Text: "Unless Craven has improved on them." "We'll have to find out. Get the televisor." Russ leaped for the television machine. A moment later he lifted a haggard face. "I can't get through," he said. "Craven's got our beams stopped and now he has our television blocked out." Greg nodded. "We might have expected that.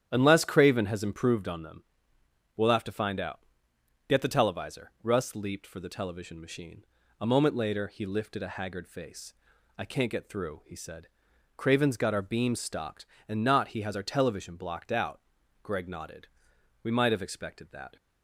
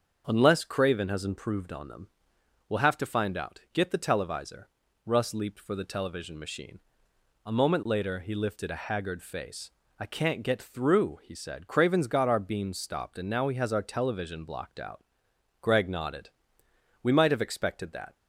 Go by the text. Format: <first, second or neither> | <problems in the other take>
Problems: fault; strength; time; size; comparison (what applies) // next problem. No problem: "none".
second | starts louder than the rest; strong; until 1.1 s; 10 dB; also in the second // says "not" for "now"; at 13.4 s